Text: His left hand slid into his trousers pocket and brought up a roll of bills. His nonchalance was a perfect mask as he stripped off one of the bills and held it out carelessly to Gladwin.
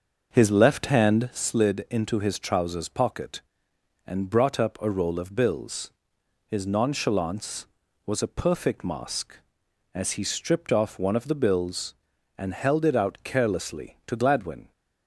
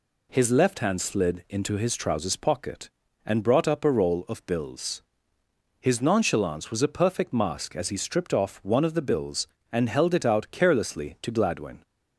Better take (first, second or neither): second